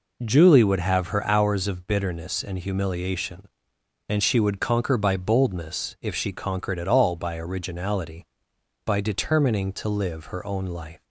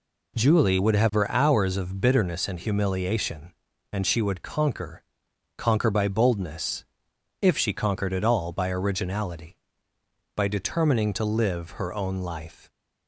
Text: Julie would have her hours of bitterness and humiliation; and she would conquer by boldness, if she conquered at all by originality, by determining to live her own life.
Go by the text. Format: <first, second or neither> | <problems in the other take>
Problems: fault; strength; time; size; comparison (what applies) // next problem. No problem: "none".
first | says "conquer" twice; at 5.5 s